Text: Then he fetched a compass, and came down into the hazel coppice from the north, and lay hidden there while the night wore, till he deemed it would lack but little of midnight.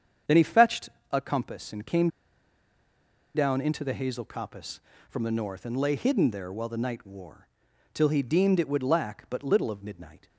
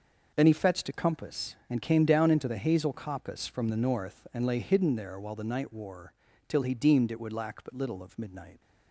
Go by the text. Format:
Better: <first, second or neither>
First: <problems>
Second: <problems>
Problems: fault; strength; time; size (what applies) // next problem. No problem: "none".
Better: second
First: starts louder than the rest; strong; until 1.4 s; 7.5 dB // pauses between "fetched" and "a"; slight; at 0.8 s; 0.20 s long // pauses between "came" and "down"; strong; at 2.0 s; 1.2 s long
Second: starts louder than the rest; noticeable; until 1.3 s; 6 dB